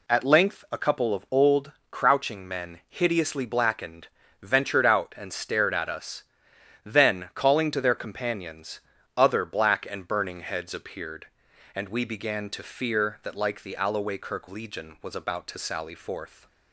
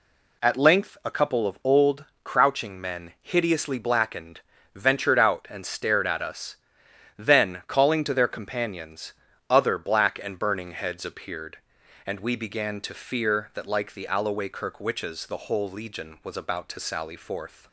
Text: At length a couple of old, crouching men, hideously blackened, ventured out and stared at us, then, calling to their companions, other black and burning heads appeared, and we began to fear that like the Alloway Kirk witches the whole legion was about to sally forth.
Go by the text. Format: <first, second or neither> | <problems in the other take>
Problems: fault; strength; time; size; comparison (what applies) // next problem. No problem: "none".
second | skips "witches the whole"; at 14.4 s